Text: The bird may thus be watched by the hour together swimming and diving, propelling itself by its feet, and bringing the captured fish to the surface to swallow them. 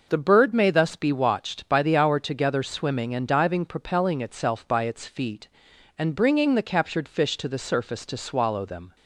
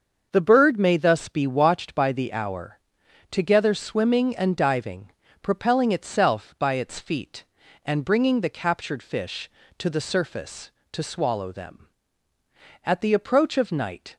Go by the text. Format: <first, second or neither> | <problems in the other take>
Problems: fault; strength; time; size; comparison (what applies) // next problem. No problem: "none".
first | starts louder than the rest; until 1.3 s; 6.5 dB // pauses between "hour" and "together"; noticeable; at 2.7 s; 0.50 s long // goes on to say "At the approach of night"; noticeable; from 12.8 s on; 1.3 s long